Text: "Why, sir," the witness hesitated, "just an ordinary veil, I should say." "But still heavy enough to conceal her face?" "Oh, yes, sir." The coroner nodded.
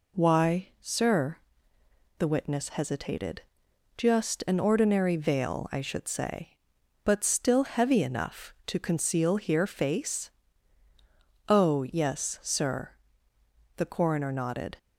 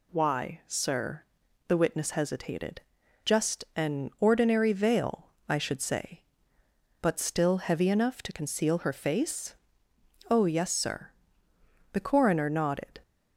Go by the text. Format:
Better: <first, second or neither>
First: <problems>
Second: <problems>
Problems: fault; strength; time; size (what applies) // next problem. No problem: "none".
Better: second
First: says "here" for "her"; at 9.3 s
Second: none